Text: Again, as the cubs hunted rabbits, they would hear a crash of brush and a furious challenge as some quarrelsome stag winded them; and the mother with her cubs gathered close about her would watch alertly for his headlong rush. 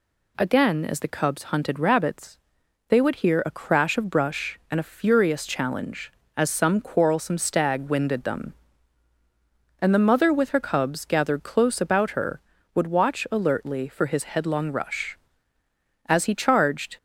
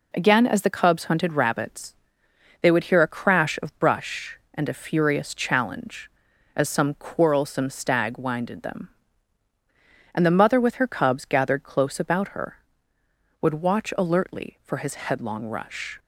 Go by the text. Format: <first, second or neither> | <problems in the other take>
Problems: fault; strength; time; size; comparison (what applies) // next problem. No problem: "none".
second | goes on to say "As he charged"; noticeable; from 16.0 s on; 0.90 s long